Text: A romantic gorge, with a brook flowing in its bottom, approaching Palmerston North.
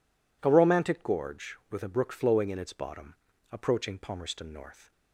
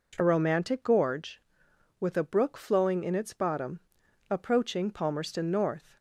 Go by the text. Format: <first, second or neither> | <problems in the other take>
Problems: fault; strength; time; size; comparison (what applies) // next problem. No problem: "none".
first | changes voice at "romantic"; from 0.2 s on; 5.7 s long